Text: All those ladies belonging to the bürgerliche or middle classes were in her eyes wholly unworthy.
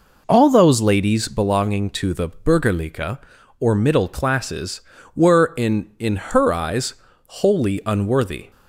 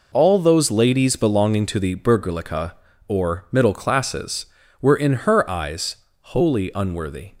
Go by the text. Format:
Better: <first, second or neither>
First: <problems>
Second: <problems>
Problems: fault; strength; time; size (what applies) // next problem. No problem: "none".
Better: second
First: says "in" twice; at 5.9 s // pauses between "eyes" and "wholly"; slight; at 6.9 s; 0.32 s long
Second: pauses between "eyes" and "wholly"; slight; at 5.9 s; 0.24 s long